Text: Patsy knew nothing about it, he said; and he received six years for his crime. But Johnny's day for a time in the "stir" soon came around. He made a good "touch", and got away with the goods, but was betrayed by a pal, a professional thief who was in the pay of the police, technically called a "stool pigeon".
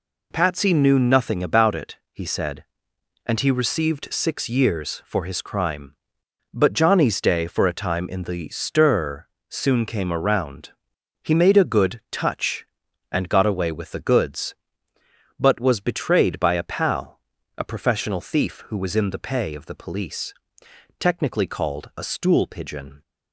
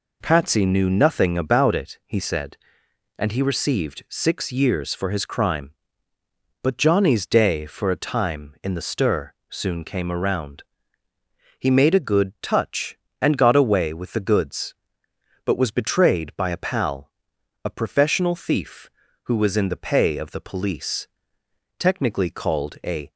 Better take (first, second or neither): first